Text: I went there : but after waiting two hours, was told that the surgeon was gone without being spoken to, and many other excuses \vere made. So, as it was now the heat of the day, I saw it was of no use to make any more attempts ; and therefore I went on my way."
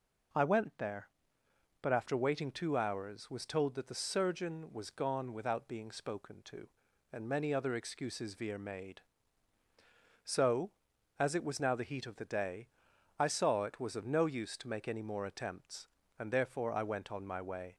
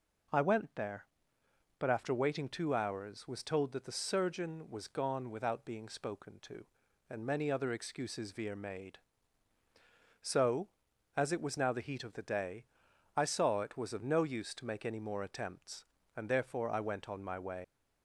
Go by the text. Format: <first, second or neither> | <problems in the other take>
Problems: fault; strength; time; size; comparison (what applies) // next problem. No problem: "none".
first | leaves "way" unfinished; at 17.6 s; 75 ms